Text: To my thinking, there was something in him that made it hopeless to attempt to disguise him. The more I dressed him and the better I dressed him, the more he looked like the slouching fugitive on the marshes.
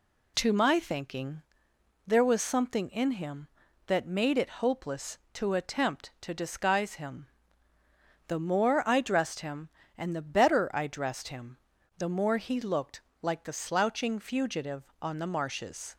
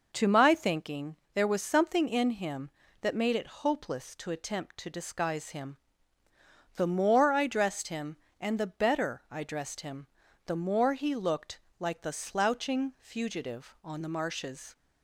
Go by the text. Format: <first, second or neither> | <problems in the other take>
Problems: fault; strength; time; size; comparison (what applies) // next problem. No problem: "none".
neither | pauses between "looked" and "like"; slight; the same in both